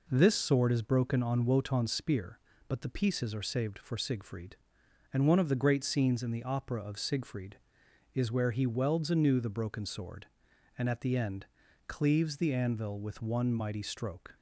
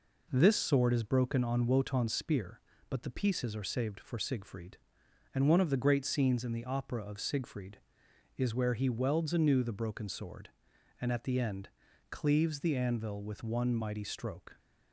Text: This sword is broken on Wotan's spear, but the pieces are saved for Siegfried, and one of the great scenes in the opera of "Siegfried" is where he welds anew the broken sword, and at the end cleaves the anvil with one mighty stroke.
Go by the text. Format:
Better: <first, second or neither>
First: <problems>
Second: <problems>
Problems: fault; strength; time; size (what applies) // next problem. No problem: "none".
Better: neither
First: pauses between "end" and "cleaves"; at 11.4 s; 0.42 s long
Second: pauses between "end" and "cleaves"; at 11.6 s; 0.42 s long